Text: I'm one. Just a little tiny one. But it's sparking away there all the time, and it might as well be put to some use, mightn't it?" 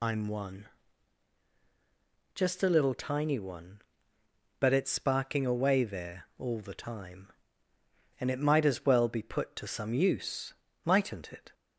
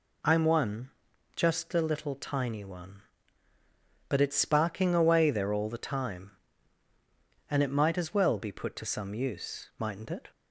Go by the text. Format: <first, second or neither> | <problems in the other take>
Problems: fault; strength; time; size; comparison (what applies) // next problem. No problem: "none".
second | loses the start of "I'm"; at 0.0 s; 35 ms